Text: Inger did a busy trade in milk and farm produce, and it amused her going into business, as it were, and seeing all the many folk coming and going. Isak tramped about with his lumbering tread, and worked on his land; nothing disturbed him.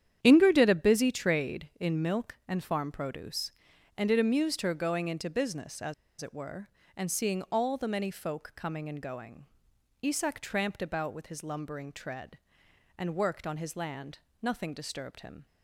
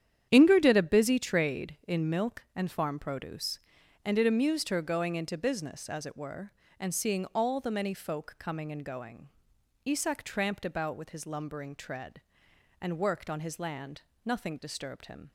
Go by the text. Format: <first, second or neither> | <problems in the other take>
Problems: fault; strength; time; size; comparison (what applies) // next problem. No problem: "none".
second | starts louder than the rest; strong; until 1.2 s; 9.5 dB; strong in the second // pauses between "as" and "it"; slight; at 5.9 s; 0.27 s long